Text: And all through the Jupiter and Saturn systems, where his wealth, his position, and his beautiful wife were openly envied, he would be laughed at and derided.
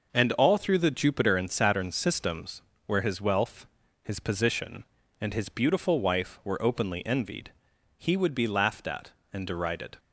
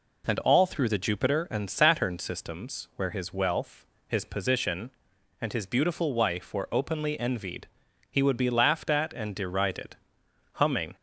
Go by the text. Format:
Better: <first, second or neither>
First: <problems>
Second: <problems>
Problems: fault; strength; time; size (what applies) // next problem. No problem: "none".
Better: first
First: none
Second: goes on to say "Humming"; slight; from 10.5 s on; 0.42 s long